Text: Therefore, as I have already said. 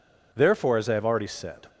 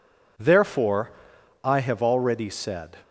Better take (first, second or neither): first